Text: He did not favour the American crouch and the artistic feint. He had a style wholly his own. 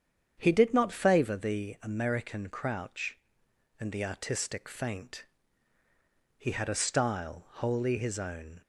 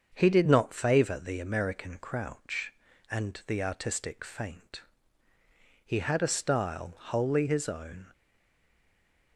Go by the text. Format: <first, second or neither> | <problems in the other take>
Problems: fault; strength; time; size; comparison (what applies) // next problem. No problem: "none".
first | starts louder than the rest; until 1.1 s; 7 dB; strong in the first // stays silent after the last word; noticeable; from 8.1 s on; 1.2 s long